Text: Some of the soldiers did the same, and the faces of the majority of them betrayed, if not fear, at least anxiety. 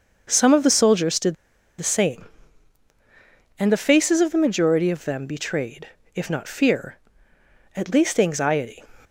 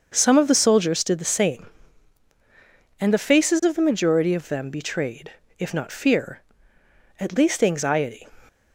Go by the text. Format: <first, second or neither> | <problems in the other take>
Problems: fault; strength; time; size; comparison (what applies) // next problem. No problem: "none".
second | starts louder than the rest; until 1.3 s; 6 dB; also in the second // pauses between "did" and "the"; noticeable; at 1.3 s; 0.46 s long